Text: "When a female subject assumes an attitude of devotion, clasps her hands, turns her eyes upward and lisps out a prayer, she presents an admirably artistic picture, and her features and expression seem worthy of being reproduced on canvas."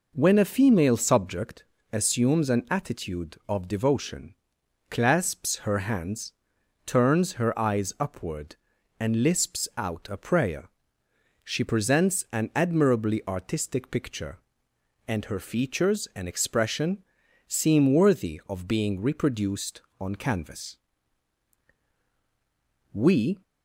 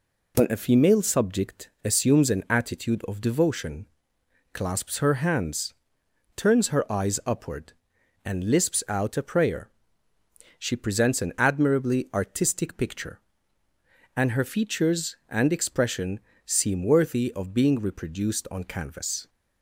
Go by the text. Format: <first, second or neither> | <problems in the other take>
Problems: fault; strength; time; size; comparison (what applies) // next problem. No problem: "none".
second | pauses between "subject" and "assumes"; slight; at 1.6 s; 0.28 s long // pauses between "expression" and "seem"; noticeable; at 17.0 s; 0.46 s long; slight in the second // goes on to say "We"; from 22.9 s on; 0.50 s long